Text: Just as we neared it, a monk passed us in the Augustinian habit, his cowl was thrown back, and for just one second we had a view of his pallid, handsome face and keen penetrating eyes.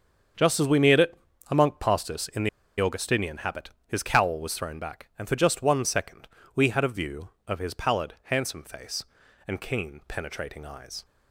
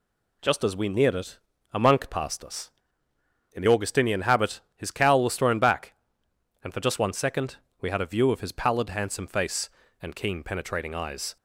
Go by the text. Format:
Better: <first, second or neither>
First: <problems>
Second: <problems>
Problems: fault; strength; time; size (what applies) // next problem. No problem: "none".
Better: second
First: starts louder than the rest; until 1.7 s; 7 dB // pauses between "the" and "Augustinian"; slight; at 2.4 s; 0.31 s long // pauses between "second" and "we"; slight; at 6.2 s; 0.28 s long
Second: pauses between "second" and "we"; slight; at 7.5 s; 0.24 s long